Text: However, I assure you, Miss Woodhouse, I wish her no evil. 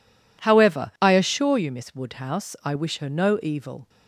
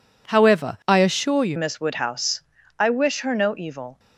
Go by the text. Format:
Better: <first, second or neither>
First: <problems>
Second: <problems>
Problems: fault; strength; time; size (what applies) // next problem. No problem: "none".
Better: first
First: none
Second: changes voice at "Miss"; from 1.5 s on; 2.4 s long